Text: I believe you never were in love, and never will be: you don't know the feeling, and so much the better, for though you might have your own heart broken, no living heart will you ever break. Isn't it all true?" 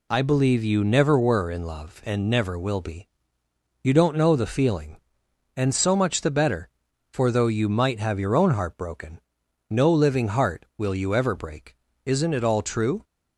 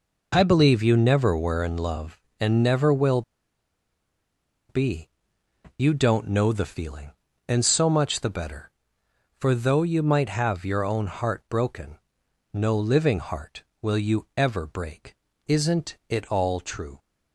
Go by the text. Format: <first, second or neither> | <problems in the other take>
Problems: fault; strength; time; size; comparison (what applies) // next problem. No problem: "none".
first | pauses between "will" and "be"; strong; at 3.2 s; 1.4 s long